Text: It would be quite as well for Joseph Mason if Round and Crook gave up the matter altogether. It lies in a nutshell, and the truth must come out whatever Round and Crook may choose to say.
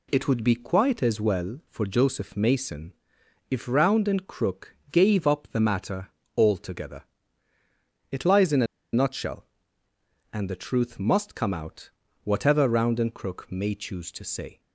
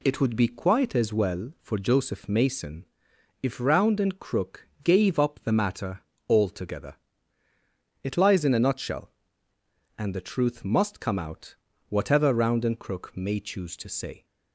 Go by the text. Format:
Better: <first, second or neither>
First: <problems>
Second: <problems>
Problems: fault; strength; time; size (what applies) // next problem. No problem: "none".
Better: second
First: pauses between "Mason" and "if"; noticeable; at 2.9 s; 0.58 s long // pauses between "matter" and "altogether"; slight; at 6.0 s; 0.28 s long // pauses between "a" and "nutshell"; slight; at 8.6 s; 0.28 s long // pauses between "out" and "whatever"; slight; at 11.8 s; 0.36 s long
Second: pauses between "Mason" and "if"; noticeable; at 2.8 s; 0.58 s long // pauses between "matter" and "altogether"; slight; at 5.9 s; 0.28 s long // pauses between "out" and "whatever"; slight; at 11.5 s; 0.36 s long